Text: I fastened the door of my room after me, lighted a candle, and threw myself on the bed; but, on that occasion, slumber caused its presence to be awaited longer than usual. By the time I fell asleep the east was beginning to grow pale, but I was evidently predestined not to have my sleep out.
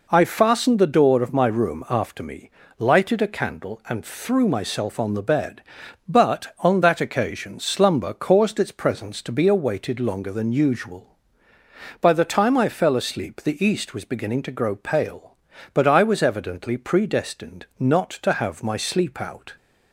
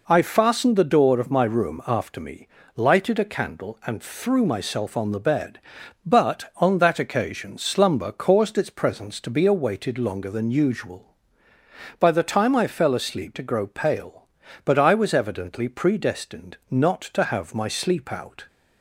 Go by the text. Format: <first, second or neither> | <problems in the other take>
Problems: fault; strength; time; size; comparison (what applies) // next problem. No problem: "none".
first | skips "the east was beginning"; at 13.3 s